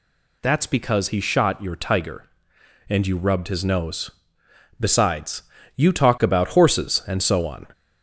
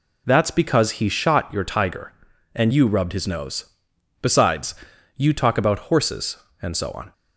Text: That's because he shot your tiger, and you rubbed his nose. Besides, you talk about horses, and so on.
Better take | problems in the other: second | gets louder; slight; throughout; 2 dB

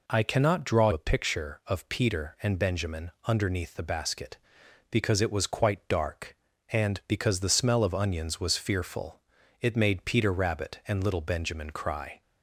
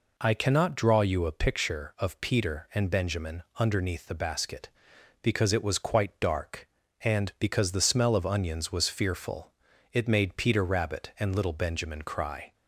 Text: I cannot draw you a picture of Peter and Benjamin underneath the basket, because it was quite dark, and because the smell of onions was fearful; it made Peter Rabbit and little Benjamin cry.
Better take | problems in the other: second | skips "you"; at 0.9 s // pauses between "Benjamin" and "underneath"; slight; at 3.1 s; 0.16 s long; slight in the second

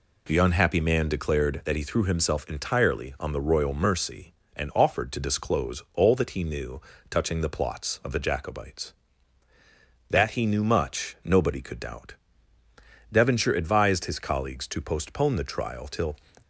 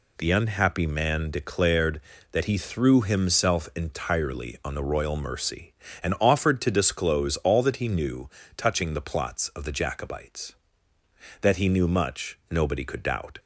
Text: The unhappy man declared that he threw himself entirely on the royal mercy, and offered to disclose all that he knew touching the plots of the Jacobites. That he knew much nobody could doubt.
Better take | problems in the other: second | pauses between "knew" and "touching"; slight; at 6.7 s; 0.30 s long; slight in the second // goes on to say "Devonshire advised his colleagues to postpone the trial till"; strong; from 13.1 s on; 3.0 s long

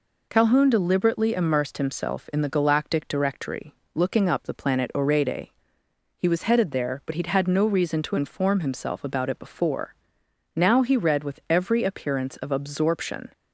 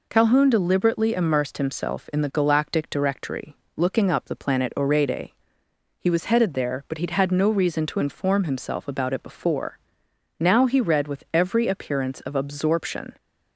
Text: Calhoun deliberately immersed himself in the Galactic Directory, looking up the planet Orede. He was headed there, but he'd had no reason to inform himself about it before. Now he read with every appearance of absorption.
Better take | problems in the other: neither | none

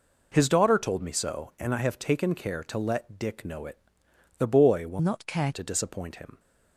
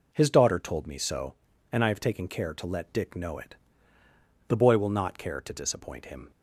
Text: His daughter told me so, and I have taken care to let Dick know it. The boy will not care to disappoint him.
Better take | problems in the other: second | changes voice from "not" to "care"; from 5.0 to 5.5 s; 0.5 s long

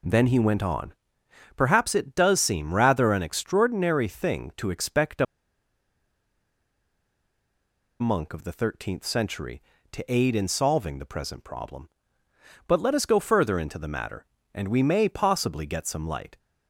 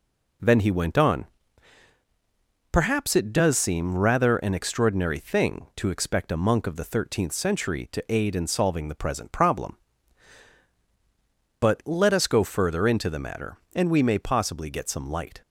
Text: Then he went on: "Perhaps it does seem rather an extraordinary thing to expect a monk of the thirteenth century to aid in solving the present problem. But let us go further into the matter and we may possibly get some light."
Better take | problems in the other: second | pauses between "a" and "monk"; strong; at 5.2 s; 2.7 s long

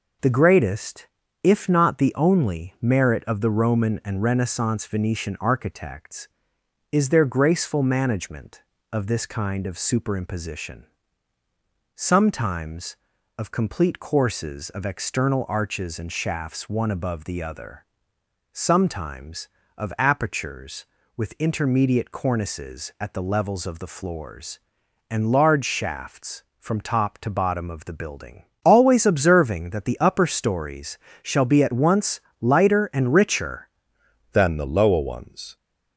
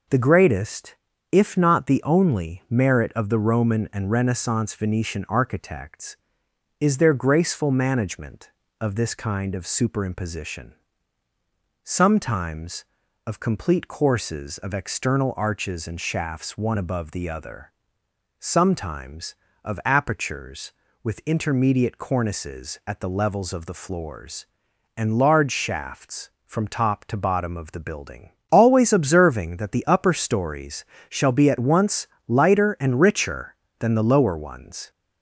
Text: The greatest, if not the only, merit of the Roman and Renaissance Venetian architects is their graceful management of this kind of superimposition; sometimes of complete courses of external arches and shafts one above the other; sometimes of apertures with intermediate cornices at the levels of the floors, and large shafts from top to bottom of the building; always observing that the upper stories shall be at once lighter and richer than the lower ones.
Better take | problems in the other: second | pauses between "stories" and "shall"; slight; at 30.9 s; 0.24 s long; slight in the second // pauses between "once" and "lighter"; slight; at 32.2 s; 0.20 s long; slight in the second // changes voice at "than"; from 34.3 s on; 1.2 s long

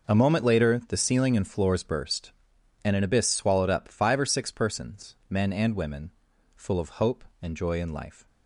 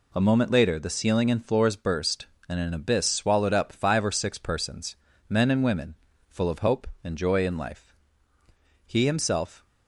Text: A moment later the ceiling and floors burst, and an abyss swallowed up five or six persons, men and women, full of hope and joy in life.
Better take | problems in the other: first | goes on to say "He himself"; noticeable; from 8.8 s on; 0.78 s long

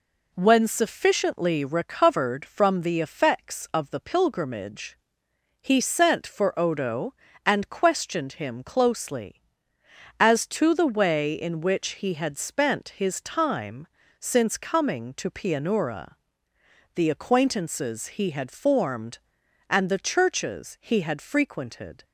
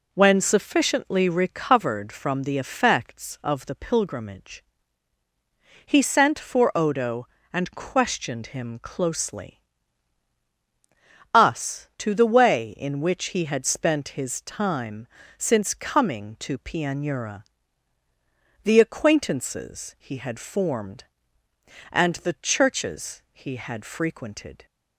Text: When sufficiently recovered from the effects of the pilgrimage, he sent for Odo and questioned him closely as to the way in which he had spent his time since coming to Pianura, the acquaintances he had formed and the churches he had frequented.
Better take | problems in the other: first | says "us" for "as"; at 11.3 s // pauses between "time" and "since"; slight; at 15.0 s; 0.30 s long; slight in the first

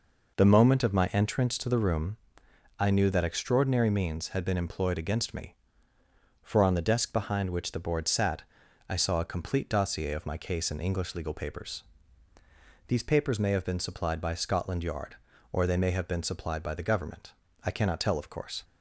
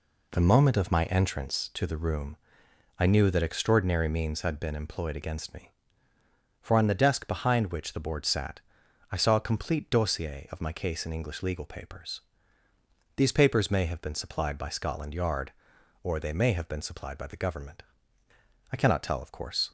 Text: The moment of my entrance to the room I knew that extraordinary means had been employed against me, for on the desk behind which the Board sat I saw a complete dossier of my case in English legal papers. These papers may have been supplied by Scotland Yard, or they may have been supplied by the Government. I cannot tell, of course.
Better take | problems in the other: neither | pauses between "room" and "I"; noticeable; the same in both // pauses between "sat" and "I"; noticeable; the same in both

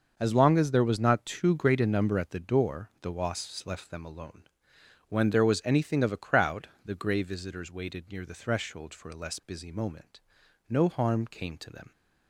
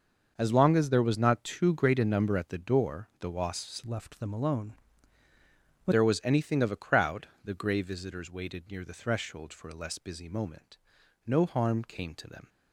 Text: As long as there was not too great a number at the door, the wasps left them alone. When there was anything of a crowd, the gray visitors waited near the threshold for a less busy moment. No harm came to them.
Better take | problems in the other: first | starts louder than the rest; until 1.3 s; 6.5 dB; also in the first // changes voice from "left" to "When"; from 3.8 to 5.9 s; 2.1 s long

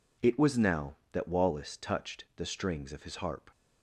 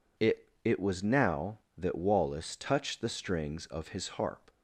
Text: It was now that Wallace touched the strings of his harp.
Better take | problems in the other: first | says "It" twice; at 0.6 s

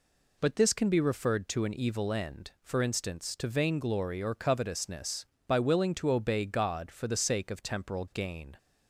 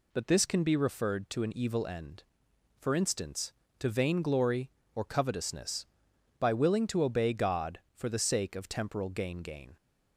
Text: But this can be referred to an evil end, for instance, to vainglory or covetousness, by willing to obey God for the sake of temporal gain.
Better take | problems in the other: first | says "gain" twice; at 9.3 s

